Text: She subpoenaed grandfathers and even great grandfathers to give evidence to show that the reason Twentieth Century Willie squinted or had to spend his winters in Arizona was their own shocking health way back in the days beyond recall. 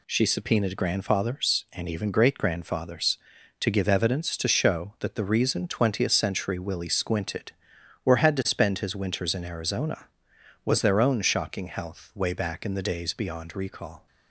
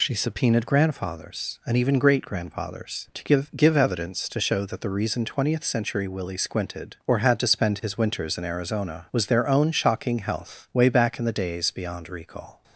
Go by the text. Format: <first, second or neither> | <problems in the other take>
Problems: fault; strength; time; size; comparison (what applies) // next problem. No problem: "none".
first | says "give" twice; at 3.5 s